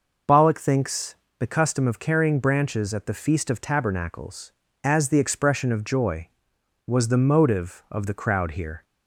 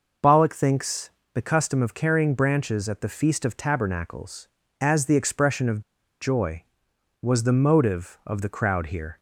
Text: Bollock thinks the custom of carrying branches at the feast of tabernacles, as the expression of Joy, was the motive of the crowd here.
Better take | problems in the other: first | pauses between "thinks" and "the"; slight; at 1.1 s; 0.24 s long; slight in the first // pauses between "of" and "Joy"; at 5.8 s; 0.38 s long

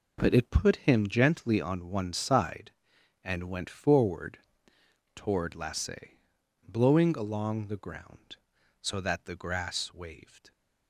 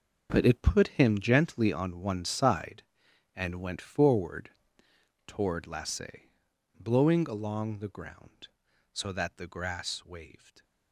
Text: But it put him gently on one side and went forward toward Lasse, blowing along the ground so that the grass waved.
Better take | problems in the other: first | gets quieter; strong; throughout; 13 dB // pauses between "forward" and "toward"; noticeable; at 4.4 s; 0.78 s long; noticeable in the first

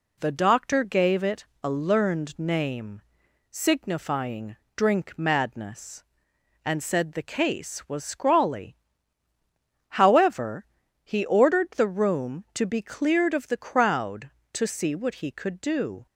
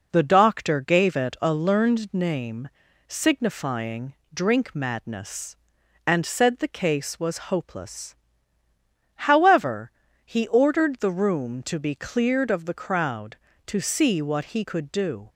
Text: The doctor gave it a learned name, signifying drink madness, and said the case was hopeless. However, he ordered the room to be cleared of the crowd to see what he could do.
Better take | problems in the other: second | pauses between "it" and "a"; slight; at 1.4 s; 0.18 s long // pauses between "signifying" and "drink"; slight; at 4.5 s; 0.22 s long; slight in the second // says "scrawly" for "hopeless"; at 8.0 s

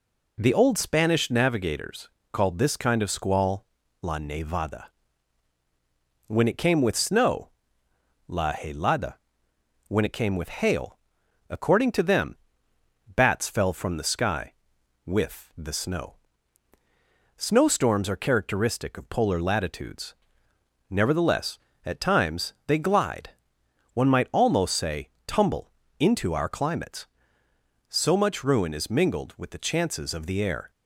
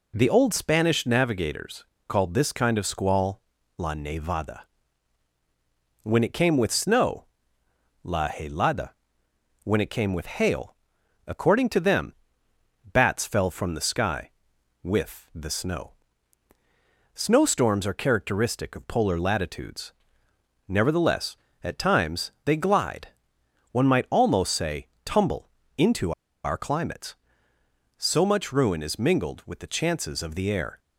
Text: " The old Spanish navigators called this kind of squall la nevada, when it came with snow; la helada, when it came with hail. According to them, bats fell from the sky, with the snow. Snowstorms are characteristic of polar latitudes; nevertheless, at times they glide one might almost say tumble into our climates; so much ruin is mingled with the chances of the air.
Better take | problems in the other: first | pauses between "navigators" and "called"; slight; at 1.8 s; 0.24 s long; slight in the first // pauses between "squall" and "la"; slight; at 3.4 s; 0.36 s long; slight in the first // pauses between "glide" and "one"; noticeable; at 23.0 s; 0.64 s long; noticeable in the first // pauses between "say" and "tumble"; slight; at 24.8 s; 0.16 s long; slight in the first // pauses between "tumble" and "into"; slight; at 25.5 s; 0.26 s long; slight in the first // pauses between "into" and "our"; slight; at 26.1 s; 0.31 s long

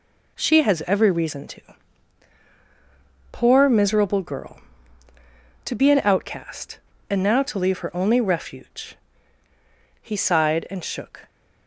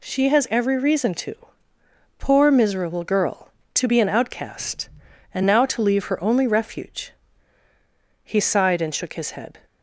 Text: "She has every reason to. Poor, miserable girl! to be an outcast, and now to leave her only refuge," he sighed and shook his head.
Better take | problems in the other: second | stops before "his head"; at 11.2 s

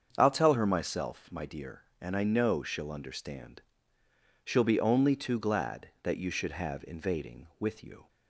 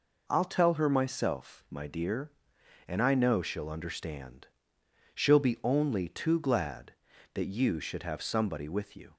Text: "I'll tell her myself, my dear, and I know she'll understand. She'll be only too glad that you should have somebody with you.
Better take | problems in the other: second | starts louder than the rest; until 1.1 s; 7 dB // says "invading" for "somebody"; at 6.8 s

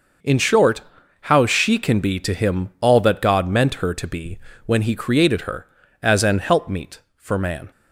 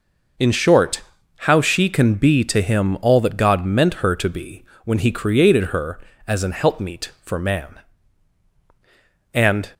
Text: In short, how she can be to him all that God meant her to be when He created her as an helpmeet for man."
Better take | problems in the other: first | pauses between "be" and "when"; slight; at 4.6 s; 0.20 s long; slight in the first // goes on to say "And"; slight; from 9.3 s on; 0.38 s long

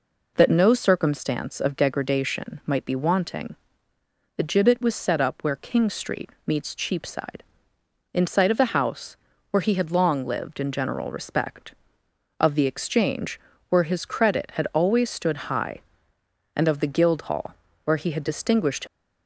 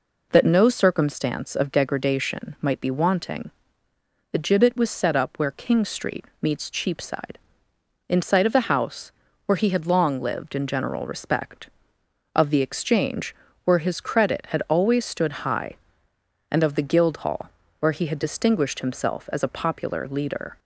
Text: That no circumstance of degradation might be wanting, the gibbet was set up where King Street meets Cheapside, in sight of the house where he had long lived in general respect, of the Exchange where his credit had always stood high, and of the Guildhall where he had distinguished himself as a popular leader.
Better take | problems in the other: second | pauses between "Street" and "meets"; slight; at 6.3 s; 0.16 s long; slight in the second // pauses between "house" and "where"; slight; at 9.1 s; 0.36 s long; slight in the second // pauses between "Exchange" and "where"; slight; at 13.3 s; 0.30 s long; slight in the second // pauses between "Guildhall" and "where"; slight; at 17.5 s; 0.30 s long; slight in the second // stops before "himself as a popular leader"; at 18.8 s

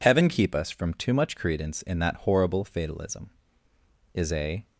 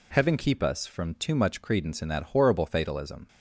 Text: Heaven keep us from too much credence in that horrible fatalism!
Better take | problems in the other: second | goes on to say "Is a"; from 4.1 s on; 0.52 s long

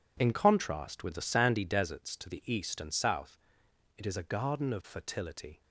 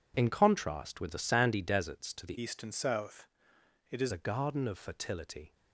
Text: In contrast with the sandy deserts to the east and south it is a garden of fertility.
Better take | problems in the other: first | changes voice from "east" to "is"; from 2.3 to 4.1 s; 1.8 s long // pauses between "south" and "it"; noticeable; at 3.2 s; 0.64 s long; noticeable in the first

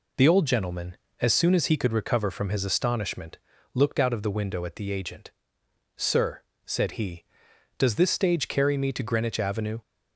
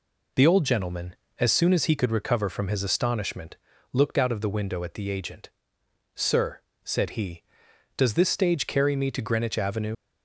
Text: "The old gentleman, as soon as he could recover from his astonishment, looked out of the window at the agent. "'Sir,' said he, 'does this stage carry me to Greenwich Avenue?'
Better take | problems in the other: first | leaves "Avenue" unfinished; at 9.9 s; 45 ms

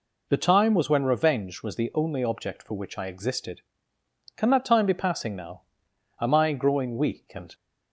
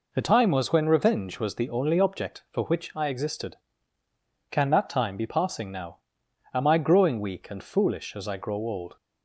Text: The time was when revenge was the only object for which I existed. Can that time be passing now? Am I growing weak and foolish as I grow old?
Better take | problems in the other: second | stops before "foolish as I grow old"; at 7.5 s

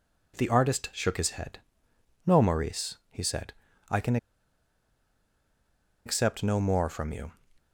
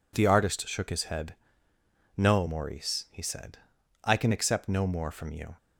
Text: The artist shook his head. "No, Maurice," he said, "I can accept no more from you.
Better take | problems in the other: second | pauses between "can" and "accept"; strong; at 4.1 s; 1.8 s long

